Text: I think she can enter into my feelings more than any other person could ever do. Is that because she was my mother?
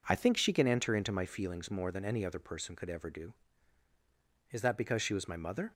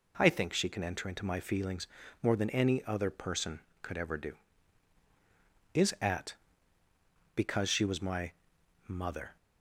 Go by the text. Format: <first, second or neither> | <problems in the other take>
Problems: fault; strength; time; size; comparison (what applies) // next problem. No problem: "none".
first | pauses between "feelings" and "more"; slight; at 1.8 s; 0.36 s long // says "at" for "that"; at 5.9 s // pauses between "my" and "mother"; noticeable; at 8.3 s; 0.56 s long